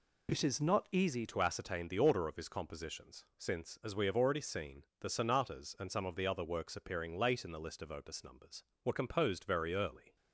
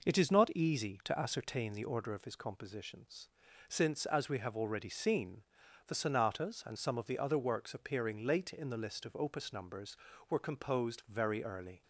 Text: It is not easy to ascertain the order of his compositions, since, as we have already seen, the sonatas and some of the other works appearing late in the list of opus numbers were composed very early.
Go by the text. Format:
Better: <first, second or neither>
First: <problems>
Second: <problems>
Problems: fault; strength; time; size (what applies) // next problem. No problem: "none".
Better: second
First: changes voice at "to"; from 1.2 s on; 8.9 s long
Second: none